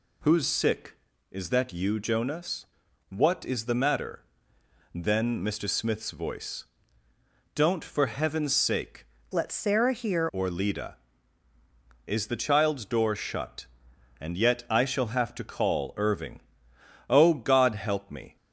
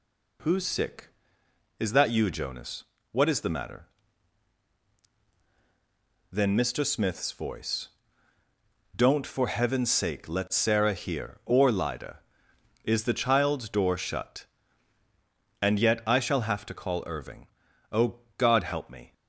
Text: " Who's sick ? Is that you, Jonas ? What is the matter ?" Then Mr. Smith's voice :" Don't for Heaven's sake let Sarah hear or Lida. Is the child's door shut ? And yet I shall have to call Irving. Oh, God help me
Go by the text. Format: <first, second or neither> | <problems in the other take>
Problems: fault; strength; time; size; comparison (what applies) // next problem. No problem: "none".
second | changes voice from "let" to "hear"; from 9.3 to 10.2 s; 0.9 s long